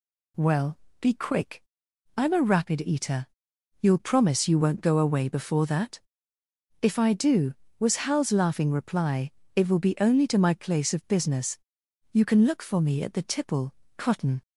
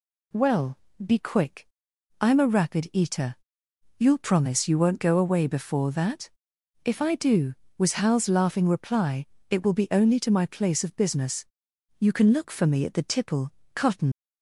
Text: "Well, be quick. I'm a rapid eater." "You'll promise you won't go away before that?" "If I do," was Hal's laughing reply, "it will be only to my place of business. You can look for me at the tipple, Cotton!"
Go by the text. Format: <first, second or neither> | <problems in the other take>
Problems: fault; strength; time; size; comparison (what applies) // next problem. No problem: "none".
first | leaves "Cotton" unfinished; at 14.1 s; 110 ms